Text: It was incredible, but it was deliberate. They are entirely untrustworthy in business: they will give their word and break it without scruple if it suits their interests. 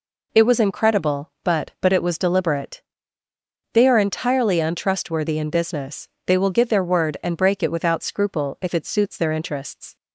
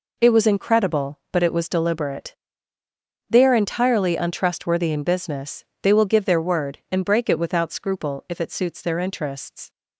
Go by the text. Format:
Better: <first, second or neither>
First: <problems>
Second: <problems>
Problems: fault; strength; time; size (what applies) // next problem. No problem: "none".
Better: second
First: says "but" twice; at 1.8 s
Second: none